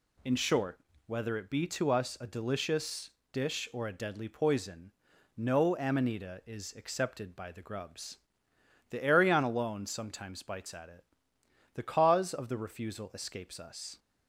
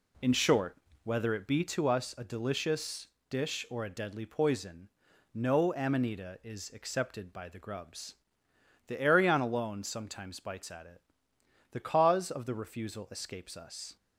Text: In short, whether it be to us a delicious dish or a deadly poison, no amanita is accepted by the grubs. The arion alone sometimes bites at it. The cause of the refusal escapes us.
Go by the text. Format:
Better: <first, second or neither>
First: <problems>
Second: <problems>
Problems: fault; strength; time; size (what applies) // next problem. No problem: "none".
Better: first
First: pauses between "delicious" and "dish"; slight; at 3.1 s; 0.22 s long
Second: starts louder than the rest; slight; until 1.7 s; 2 dB // pauses between "delicious" and "dish"; slight; at 3.0 s; 0.22 s long